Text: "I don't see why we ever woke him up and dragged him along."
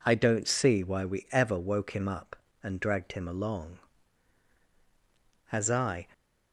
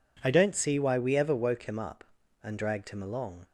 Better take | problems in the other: second | goes on to say "As I"; from 5.5 s on; 0.56 s long

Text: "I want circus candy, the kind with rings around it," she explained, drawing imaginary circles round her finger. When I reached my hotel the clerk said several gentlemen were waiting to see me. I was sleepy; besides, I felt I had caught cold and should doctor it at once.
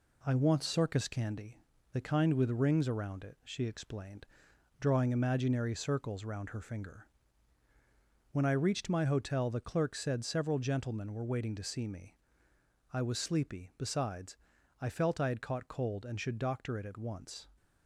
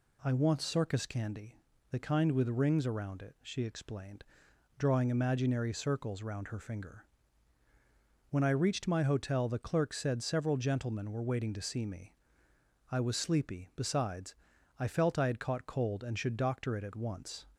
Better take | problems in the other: second | gets quieter; noticeable; throughout; 4 dB

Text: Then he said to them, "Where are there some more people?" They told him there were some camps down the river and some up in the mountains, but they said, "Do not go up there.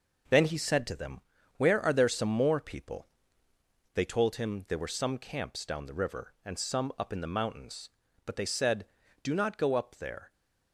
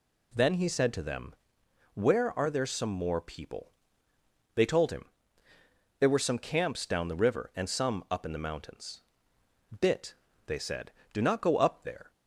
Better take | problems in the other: first | pauses between "him" and "there"; noticeable; at 5.0 s; 0.94 s long // says "bit" for "but"; at 9.7 s

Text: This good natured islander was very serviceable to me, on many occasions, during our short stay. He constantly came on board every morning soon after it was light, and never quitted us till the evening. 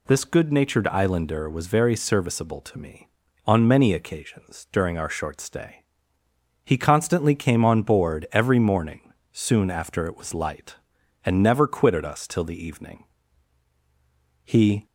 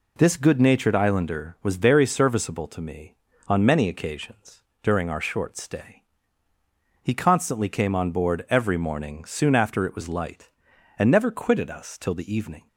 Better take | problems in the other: second | pauses between "morning" and "soon"; slight; at 9.1 s; 0.18 s long // goes on to say "He"; slight; from 14.4 s on; 0.42 s long

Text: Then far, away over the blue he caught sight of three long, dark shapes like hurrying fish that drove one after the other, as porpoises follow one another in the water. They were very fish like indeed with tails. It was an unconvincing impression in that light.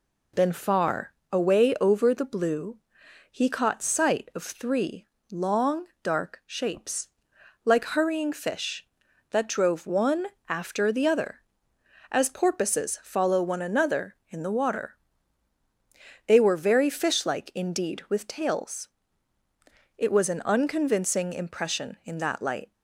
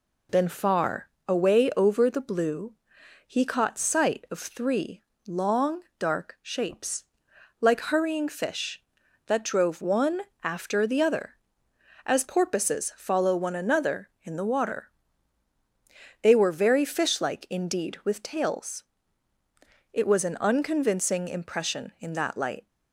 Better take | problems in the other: neither | pauses between "blue" and "he"; noticeable; the same in both // pauses between "three" and "long"; slight; the same in both // pauses between "shapes" and "like"; noticeable; the same in both // pauses between "one" and "after"; slight; the same in both

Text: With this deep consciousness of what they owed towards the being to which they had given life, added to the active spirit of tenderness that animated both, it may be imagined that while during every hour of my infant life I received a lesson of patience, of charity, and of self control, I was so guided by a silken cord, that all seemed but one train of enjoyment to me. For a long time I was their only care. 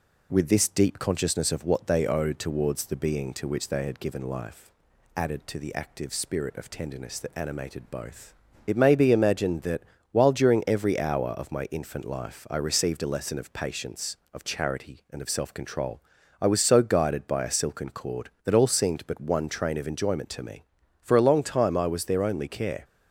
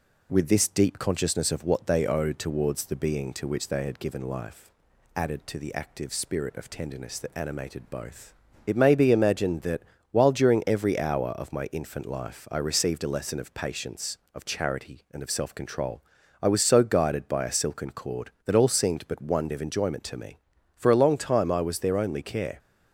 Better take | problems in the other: first | pauses between "that" and "while"; slight; at 9.8 s; 0.32 s long; slight in the first // skips "train"; at 19.5 s

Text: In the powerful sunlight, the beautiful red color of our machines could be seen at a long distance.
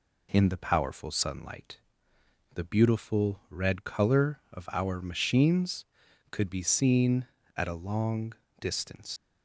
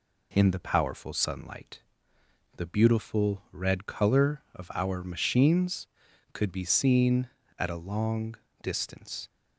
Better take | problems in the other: second | pauses between "long" and "distance"; slight; at 8.3 s; 0.26 s long; slight in the second // leaves "distance" unfinished; at 9.1 s; 95 ms

